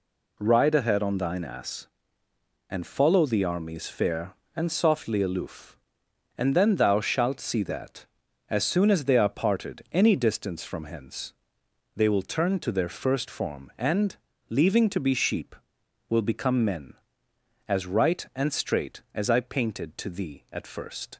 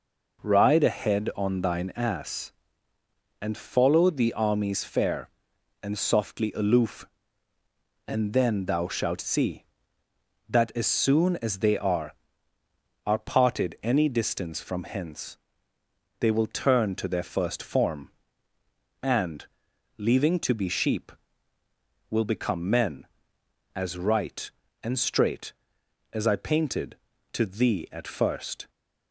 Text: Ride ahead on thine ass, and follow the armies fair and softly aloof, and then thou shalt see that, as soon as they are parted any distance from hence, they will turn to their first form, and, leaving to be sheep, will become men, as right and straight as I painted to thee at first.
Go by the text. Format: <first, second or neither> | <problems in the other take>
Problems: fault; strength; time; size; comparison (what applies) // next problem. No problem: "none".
first | says "are" twice; at 13.0 s